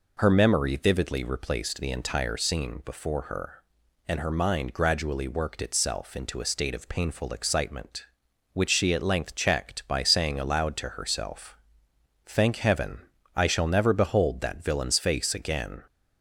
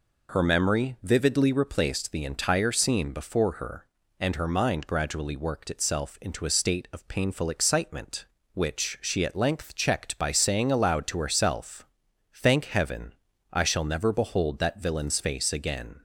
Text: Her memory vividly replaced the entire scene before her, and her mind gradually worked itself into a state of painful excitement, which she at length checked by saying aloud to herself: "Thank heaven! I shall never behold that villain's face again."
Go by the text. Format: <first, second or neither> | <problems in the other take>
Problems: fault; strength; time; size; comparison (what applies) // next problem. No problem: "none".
neither | none